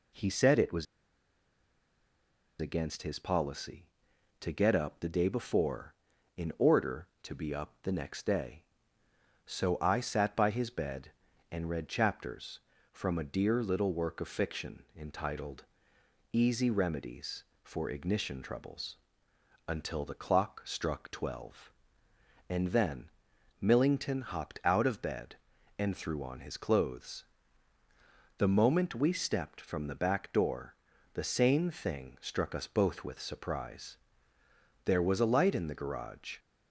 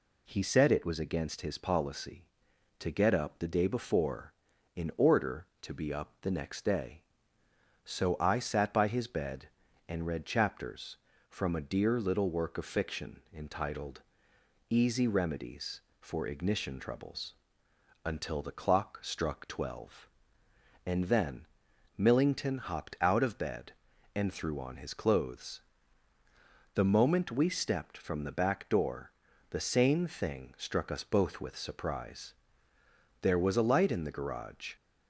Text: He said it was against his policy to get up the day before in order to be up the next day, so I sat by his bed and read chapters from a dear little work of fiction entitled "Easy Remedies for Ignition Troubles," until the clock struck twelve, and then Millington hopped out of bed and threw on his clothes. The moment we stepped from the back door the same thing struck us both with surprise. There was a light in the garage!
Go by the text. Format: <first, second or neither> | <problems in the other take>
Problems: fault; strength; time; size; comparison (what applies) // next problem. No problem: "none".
second | pauses between "was" and "against"; strong; at 0.8 s; 1.7 s long // pauses between "entitled" and "Easy"; noticeable; at 15.6 s; 0.70 s long; noticeable in the second // pauses between "then" and "Millington"; noticeable; at 23.0 s; 0.52 s long; noticeable in the second // pauses between "door" and "the"; at 30.7 s; 0.40 s long; also in the second